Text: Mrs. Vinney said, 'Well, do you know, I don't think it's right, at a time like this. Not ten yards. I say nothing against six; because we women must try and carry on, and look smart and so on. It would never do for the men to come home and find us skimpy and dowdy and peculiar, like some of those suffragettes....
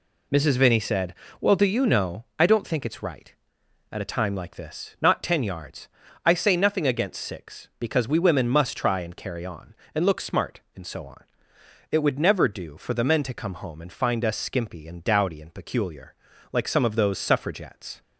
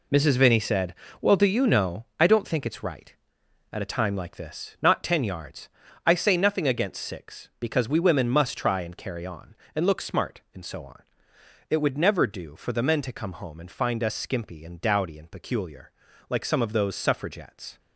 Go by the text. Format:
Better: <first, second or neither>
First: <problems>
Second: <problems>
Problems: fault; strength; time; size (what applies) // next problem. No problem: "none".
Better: first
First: none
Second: gets quieter; strong; throughout; 9 dB